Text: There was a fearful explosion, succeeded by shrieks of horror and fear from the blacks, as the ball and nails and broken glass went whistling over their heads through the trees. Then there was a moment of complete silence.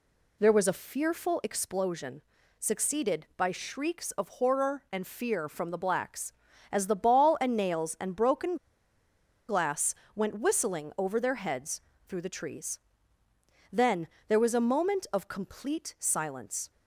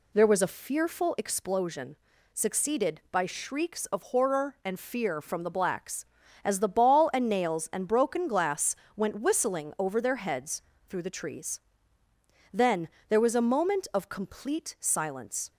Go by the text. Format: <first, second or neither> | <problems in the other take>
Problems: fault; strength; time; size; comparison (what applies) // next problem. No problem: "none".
second | pauses between "broken" and "glass"; noticeable; at 8.5 s; 0.93 s long // pauses between "glass" and "went"; slight; at 9.9 s; 0.22 s long; slight in the second // pauses between "heads" and "through"; slight; at 11.7 s; 0.28 s long; slight in the second // pauses between "Then" and "there"; slight; at 14.0 s; 0.20 s long; slight in the second